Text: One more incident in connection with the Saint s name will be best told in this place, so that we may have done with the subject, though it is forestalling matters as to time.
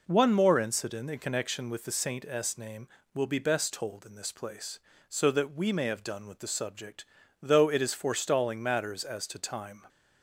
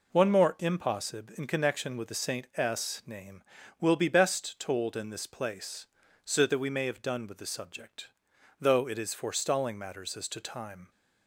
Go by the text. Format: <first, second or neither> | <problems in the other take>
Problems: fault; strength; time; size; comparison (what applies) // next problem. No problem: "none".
first | says "impossib" for "incident"; at 0.5 s